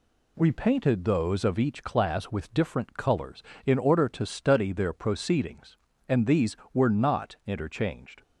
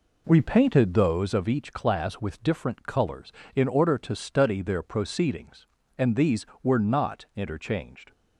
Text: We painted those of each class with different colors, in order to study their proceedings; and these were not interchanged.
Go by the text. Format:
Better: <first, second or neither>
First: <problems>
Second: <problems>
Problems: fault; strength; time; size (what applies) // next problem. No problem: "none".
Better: first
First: none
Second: starts louder than the rest; until 1.2 s; 4 dB